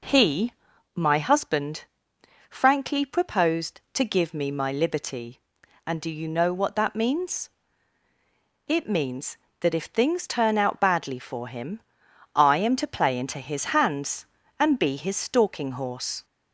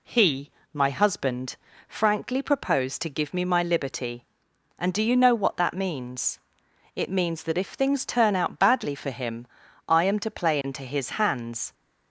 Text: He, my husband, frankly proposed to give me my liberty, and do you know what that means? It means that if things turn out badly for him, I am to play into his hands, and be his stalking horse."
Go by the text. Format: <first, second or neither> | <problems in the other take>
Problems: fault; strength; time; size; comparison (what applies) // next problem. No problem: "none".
first | stops before "and be his stalking horse"; at 11.7 s